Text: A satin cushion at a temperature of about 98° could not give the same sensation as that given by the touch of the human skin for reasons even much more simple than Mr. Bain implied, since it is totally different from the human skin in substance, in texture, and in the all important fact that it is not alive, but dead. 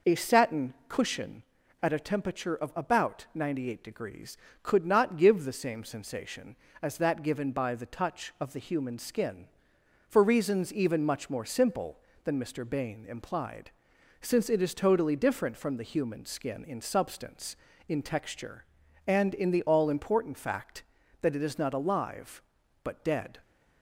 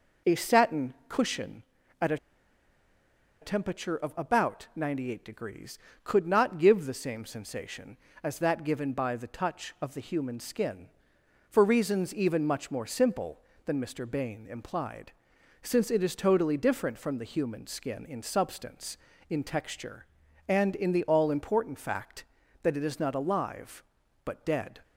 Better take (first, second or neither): first